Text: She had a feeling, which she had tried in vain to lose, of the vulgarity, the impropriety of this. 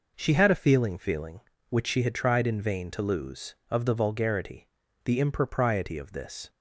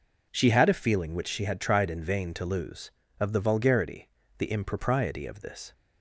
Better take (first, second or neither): second